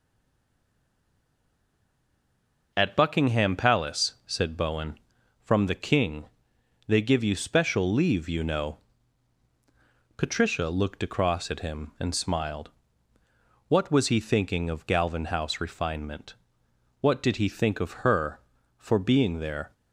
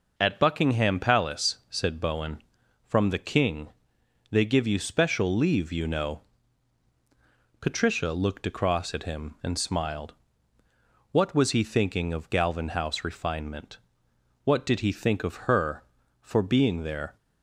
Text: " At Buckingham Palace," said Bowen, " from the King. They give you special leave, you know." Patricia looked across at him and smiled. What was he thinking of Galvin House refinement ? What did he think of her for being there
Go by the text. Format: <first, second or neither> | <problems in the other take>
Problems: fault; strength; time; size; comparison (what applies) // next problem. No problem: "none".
second | stays silent before the first word; strong; until 2.7 s; 2.7 s long